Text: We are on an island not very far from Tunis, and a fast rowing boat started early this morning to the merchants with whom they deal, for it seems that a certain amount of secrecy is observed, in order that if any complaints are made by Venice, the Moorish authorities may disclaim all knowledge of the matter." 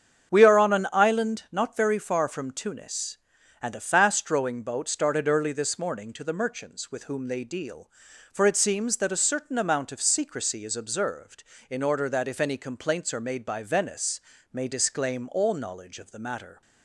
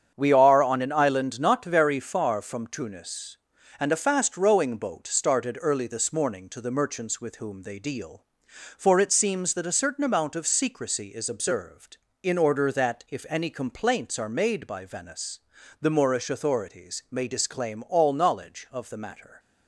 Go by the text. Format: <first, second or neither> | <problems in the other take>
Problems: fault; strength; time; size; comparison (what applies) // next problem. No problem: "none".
second | starts louder than the rest; strong; until 1.3 s; 8 dB; strong in the second // skips "the Moorish authorities"; at 14.3 s